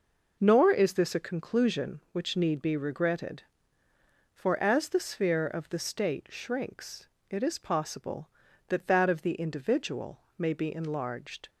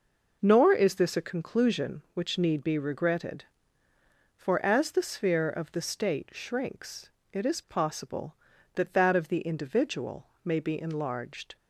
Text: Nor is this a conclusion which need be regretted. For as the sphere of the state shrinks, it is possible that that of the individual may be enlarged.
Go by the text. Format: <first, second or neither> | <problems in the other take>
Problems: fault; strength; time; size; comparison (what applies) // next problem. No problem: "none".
neither | pauses between "individual" and "may"; slight; the same in both